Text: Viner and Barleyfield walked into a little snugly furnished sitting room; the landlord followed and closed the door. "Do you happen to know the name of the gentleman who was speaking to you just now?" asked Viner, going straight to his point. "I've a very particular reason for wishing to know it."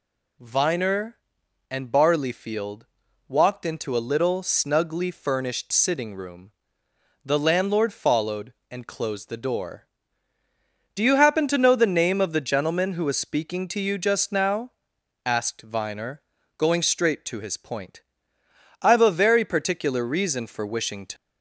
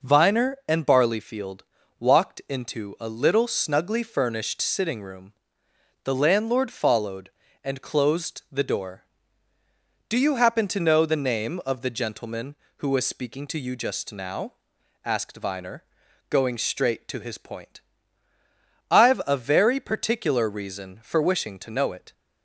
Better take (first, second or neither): second